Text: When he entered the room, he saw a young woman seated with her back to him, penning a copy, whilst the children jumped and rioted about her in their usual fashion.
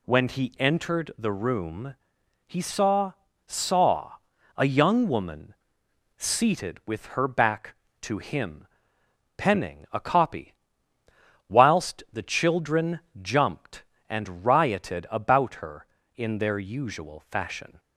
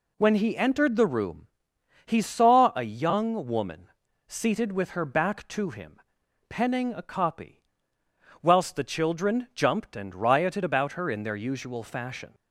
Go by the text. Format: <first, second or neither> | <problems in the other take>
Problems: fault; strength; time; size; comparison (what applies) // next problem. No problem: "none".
second | says "saw" twice; at 3.4 s // pauses between "woman" and "seated"; noticeable; at 5.5 s; 0.64 s long; also in the second // pauses between "children" and "jumped"; slight; at 12.9 s; 0.22 s long